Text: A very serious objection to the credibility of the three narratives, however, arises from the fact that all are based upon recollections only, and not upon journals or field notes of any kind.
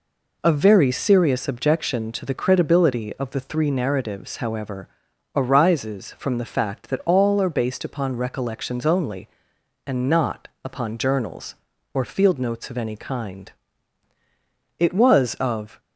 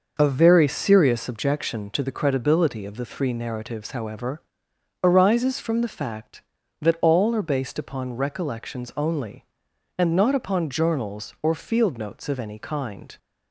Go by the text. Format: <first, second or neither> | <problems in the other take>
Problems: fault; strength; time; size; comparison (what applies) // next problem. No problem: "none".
second | pauses between "not" and "upon"; slight; at 10.4 s; 0.16 s long // goes on to say "It was of"; noticeable; from 14.7 s on; 1.0 s long